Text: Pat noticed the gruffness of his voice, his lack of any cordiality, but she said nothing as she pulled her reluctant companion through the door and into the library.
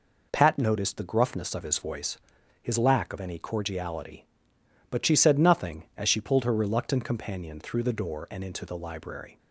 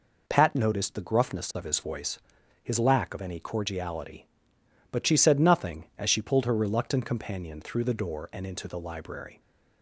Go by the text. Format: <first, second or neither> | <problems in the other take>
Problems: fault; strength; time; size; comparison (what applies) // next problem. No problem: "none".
neither | none